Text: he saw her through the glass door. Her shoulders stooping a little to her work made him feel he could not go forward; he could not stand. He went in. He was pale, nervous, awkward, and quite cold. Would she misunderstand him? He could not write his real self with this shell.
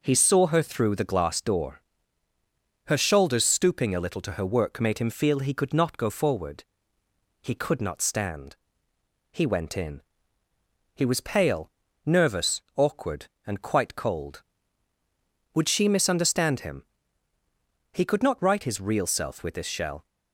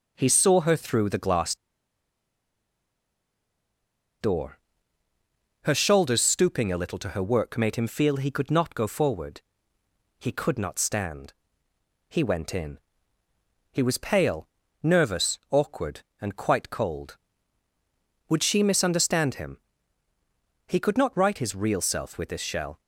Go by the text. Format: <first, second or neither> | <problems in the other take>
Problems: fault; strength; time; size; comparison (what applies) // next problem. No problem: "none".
first | pauses between "glass" and "door"; strong; at 1.5 s; 2.6 s long